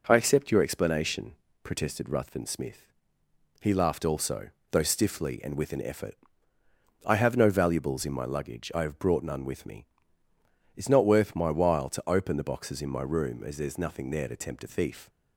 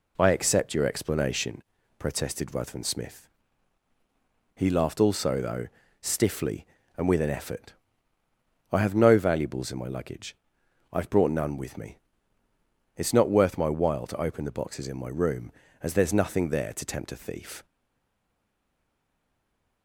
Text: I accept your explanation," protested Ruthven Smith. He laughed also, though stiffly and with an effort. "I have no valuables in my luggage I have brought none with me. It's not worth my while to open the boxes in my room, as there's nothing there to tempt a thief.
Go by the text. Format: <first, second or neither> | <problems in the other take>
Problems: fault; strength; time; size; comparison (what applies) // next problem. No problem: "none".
first | pauses between "though" and "stiffly"; slight; at 5.6 s; 0.34 s long // pauses between "luggage" and "I"; noticeable; at 10.3 s; 0.60 s long // stays silent after the last word; from 17.6 s on; 2.2 s long